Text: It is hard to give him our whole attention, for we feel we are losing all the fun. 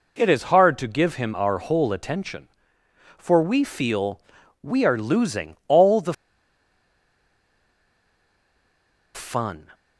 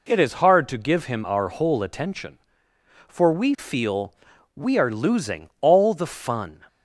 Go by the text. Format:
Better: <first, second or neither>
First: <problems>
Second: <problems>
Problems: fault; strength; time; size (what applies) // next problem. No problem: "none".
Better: second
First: pauses between "feel" and "we"; at 4.1 s; 0.44 s long // pauses between "the" and "fun"; strong; at 6.1 s; 2.9 s long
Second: pauses between "feel" and "we"; at 4.1 s; 0.44 s long